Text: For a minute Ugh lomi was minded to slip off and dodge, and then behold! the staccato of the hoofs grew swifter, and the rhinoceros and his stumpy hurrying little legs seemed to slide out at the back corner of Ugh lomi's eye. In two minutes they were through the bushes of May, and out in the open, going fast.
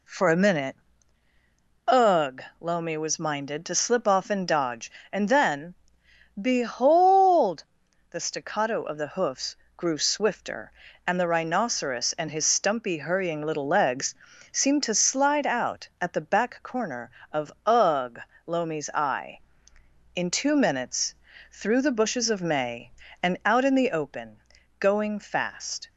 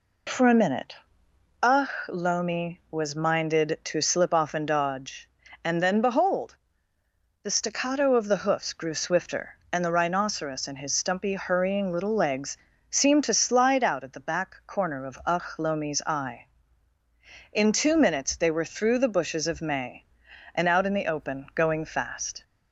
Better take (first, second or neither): second